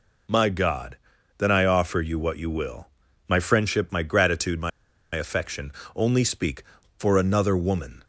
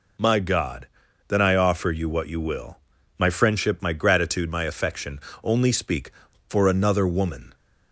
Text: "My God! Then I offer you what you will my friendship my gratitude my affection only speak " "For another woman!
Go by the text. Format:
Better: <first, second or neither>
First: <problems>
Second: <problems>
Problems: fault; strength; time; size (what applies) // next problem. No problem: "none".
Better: second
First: pauses between "will" and "my"; at 2.8 s; 0.40 s long // pauses between "my" and "affection"; at 4.7 s; 0.45 s long // pauses between "affection" and "only"; slight; at 5.7 s; 0.24 s long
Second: pauses between "will" and "my"; at 2.7 s; 0.40 s long // pauses between "affection" and "only"; slight; at 5.1 s; 0.24 s long